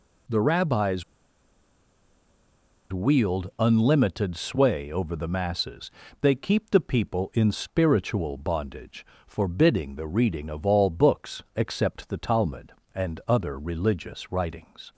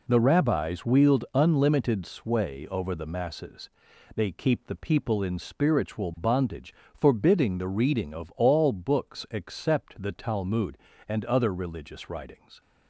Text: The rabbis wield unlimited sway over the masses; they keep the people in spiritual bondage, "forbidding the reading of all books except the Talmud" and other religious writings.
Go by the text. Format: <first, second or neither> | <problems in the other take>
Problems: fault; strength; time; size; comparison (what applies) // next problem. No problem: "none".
second | pauses between "rabbis" and "wield"; strong; at 1.0 s; 1.8 s long